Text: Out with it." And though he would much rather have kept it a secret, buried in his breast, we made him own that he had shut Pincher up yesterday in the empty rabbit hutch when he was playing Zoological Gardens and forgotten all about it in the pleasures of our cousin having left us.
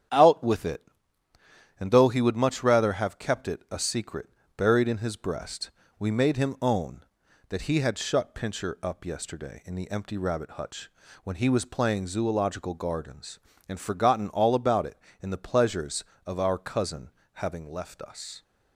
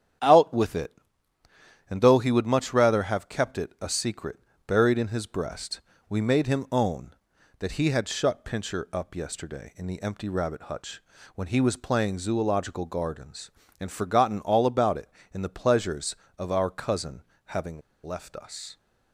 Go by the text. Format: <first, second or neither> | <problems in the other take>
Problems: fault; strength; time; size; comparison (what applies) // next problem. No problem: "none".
first | starts louder than the rest; strong; until 2.1 s; 9.5 dB; strong in the first // pauses between "hutch" and "when"; slight; at 11.0 s; 0.34 s long; slight in the first // pauses between "cousin" and "having"; slight; at 17.2 s; 0.24 s long; slight in the first // pauses between "having" and "left"; slight; at 17.8 s; 0.24 s long